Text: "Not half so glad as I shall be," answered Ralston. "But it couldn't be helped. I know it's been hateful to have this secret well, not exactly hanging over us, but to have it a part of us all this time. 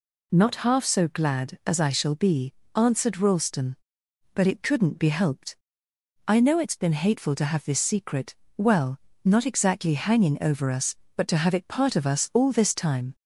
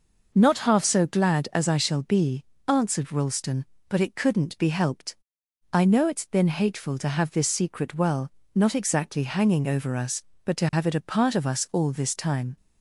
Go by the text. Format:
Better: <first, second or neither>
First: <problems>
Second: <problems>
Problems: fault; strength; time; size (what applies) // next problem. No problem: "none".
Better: second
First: pauses between "secret" and "well"; slight; at 8.3 s; 0.22 s long // skips "a"; at 11.6 s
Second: none